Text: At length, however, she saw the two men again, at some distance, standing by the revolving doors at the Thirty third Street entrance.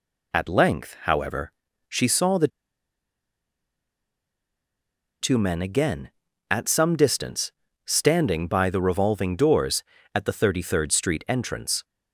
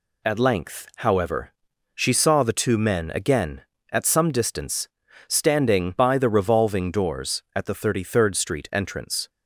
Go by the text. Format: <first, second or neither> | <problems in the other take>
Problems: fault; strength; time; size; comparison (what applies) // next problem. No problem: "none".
second | pauses between "the" and "two"; strong; at 2.4 s; 2.7 s long